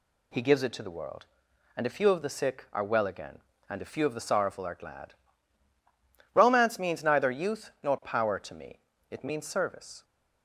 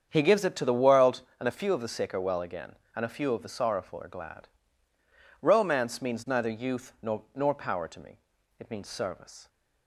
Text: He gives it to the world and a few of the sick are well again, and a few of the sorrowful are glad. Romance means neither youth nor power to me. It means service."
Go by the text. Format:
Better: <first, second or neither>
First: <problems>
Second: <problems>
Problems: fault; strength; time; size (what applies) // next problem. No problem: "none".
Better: first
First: none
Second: starts louder than the rest; strong; until 1.1 s; 7.5 dB // says "nor" twice; at 7.3 s